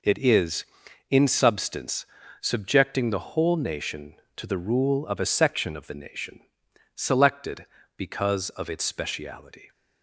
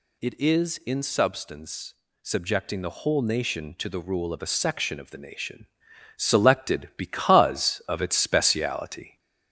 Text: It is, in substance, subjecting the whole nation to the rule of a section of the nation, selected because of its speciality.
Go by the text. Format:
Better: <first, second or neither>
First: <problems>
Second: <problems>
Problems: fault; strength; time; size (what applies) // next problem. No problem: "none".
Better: first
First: none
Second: gets louder; slight; throughout; 2 dB